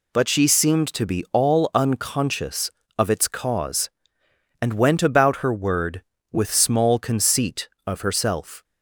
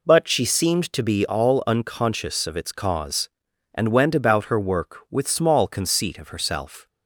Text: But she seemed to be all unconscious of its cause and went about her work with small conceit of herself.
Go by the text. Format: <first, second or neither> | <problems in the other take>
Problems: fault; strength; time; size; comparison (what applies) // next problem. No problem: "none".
second | says "word" for "work"; at 5.5 s